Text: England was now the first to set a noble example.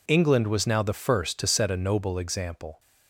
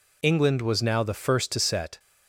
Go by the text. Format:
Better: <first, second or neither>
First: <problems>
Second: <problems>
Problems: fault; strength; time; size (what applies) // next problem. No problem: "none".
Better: first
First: none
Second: stops before "a noble example"; at 1.9 s